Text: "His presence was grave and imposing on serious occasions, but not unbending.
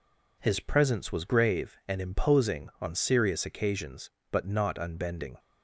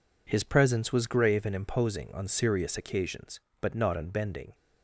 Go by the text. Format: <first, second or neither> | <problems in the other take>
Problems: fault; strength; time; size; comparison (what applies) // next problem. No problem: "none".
neither | none